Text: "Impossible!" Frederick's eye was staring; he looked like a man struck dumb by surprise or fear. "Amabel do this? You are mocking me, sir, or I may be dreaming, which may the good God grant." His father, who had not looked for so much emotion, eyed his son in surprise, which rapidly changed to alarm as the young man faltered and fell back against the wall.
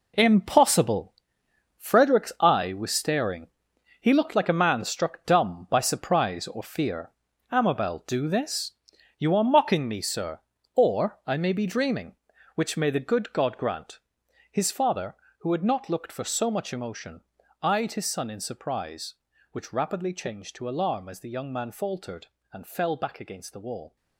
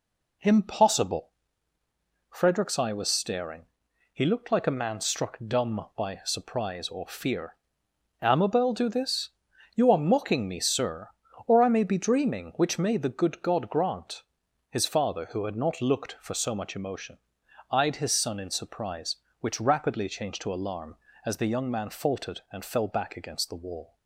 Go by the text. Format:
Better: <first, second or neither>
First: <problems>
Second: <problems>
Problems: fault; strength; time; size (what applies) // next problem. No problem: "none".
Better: second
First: gets quieter; strong; throughout; 11 dB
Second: none